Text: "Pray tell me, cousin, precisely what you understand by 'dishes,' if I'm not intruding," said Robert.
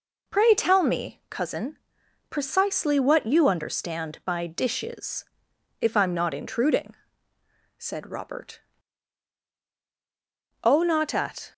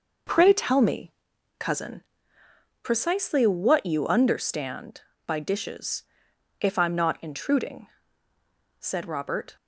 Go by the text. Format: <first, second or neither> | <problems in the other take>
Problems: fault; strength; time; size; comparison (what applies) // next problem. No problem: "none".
second | goes on to say "O not at"; noticeable; from 10.6 s on; 0.88 s long